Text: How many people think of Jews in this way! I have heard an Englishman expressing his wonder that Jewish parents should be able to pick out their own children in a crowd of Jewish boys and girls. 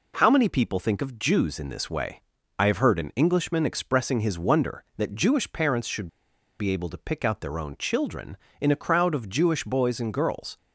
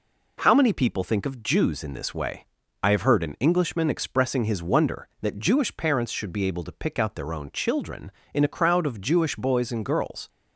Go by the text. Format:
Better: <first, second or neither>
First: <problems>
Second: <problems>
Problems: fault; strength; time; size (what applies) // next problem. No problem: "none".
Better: second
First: pauses between "should" and "be"; noticeable; at 6.0 s; 0.52 s long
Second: none